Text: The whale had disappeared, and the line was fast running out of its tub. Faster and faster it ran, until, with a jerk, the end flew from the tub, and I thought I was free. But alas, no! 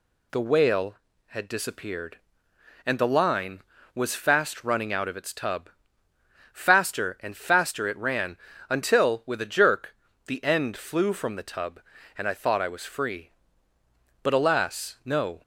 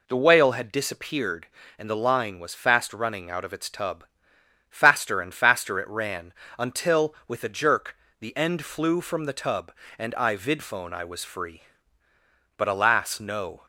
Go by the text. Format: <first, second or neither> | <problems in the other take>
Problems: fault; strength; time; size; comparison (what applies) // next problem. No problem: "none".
first | says "vidphone" for "thought"; at 10.3 s